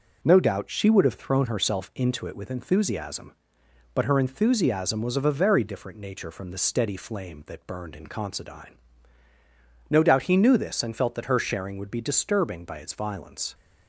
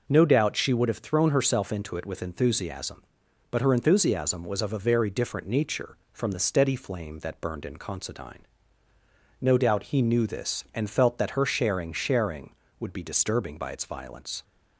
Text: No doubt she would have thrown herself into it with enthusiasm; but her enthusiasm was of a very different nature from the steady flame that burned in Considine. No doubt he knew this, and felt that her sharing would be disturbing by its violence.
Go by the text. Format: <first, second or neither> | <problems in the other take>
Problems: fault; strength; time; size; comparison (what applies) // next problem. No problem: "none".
first | says "sharing" twice; at 11.9 s